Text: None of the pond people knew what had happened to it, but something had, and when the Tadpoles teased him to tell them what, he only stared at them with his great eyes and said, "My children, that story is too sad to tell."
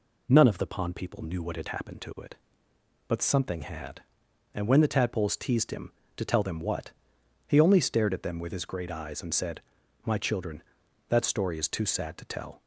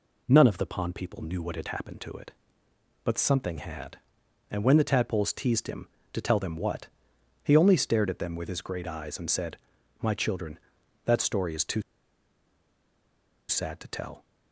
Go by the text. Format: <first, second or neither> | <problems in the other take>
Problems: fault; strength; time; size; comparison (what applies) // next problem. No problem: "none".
first | pauses between "too" and "sad"; strong; at 11.8 s; 1.6 s long